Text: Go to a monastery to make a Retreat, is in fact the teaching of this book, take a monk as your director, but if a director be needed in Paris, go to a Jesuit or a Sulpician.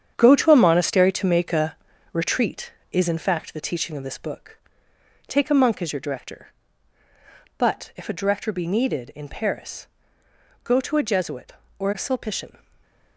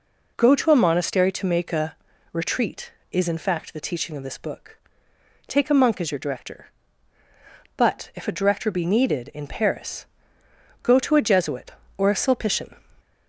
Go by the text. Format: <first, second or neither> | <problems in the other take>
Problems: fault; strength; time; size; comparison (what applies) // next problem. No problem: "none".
second | gets quieter; strong; throughout; 9 dB // pauses between "a" and "Retreat"; at 1.7 s; 0.38 s long; also in the second // stays silent after the last word; slight; from 12.5 s on; 0.6 s long